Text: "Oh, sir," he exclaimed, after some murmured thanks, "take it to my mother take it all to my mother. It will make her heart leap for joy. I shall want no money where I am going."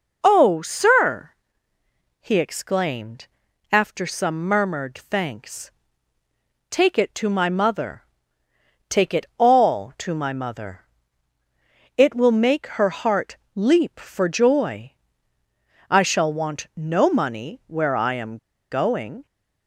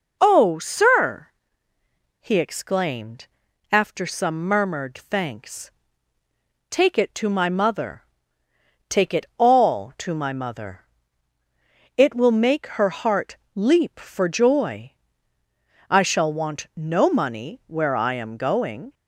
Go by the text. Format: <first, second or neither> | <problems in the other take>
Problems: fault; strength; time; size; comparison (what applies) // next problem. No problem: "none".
second | pauses between "mother" and "take"; noticeable; at 8.0 s; 0.88 s long; noticeable in the second // pauses between "heart" and "leap"; slight; at 13.3 s; 0.18 s long; slight in the second // pauses between "am" and "going"; slight; at 18.3 s; 0.33 s long